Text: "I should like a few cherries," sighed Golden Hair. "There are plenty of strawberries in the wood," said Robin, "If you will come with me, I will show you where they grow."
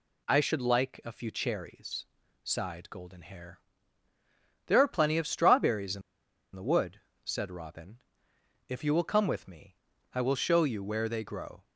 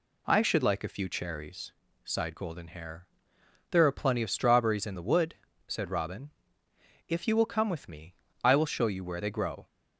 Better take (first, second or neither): second